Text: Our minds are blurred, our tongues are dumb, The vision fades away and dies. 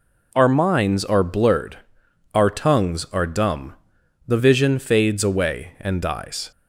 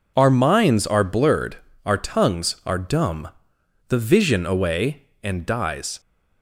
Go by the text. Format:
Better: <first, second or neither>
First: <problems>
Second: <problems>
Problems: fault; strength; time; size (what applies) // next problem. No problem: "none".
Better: first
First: none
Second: skips "fades"; at 4.4 s